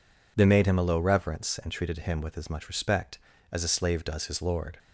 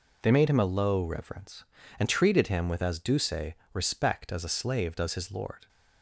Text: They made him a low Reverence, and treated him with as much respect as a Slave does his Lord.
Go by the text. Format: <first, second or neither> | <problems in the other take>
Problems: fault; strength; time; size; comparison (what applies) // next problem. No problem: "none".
first | says "duce" for "much"; at 2.9 s